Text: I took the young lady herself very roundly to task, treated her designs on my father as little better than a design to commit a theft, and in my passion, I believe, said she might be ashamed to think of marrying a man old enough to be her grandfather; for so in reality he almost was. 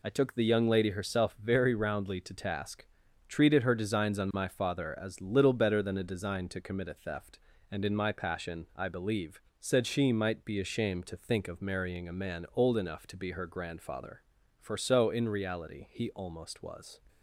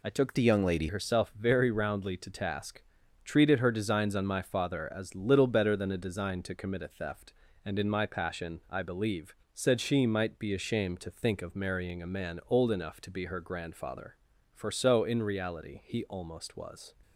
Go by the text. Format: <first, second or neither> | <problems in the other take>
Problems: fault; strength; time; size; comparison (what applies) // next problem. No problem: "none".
first | changes voice from "the" to "lady"; from 0.3 to 0.8 s; 0.5 s long